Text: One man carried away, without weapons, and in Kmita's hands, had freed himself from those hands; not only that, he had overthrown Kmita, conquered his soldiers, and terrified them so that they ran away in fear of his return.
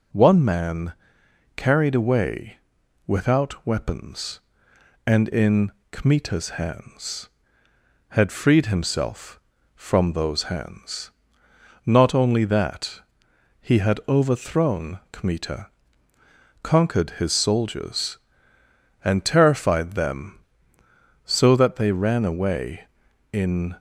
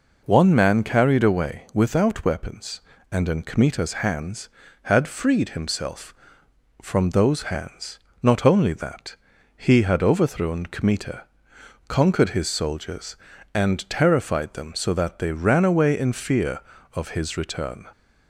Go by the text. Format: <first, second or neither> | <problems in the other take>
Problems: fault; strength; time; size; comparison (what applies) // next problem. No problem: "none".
second | pauses between "man" and "carried"; noticeable; at 0.9 s; 0.62 s long // pauses between "in" and "Kmita's"; slight; at 5.7 s; 0.20 s long // stops before "fear of his return"; at 23.7 s